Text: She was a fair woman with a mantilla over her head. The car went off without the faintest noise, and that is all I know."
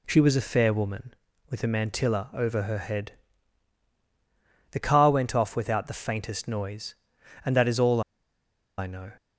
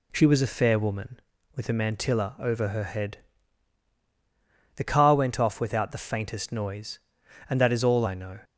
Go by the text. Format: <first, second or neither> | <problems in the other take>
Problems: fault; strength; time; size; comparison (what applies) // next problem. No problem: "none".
second | pauses between "all" and "I"; noticeable; at 8.0 s; 0.77 s long